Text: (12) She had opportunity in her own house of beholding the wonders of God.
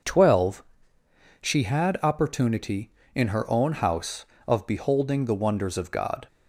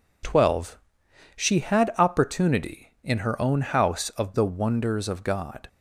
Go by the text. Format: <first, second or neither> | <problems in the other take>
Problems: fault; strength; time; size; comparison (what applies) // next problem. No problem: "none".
first | skips "beholding"; at 4.3 s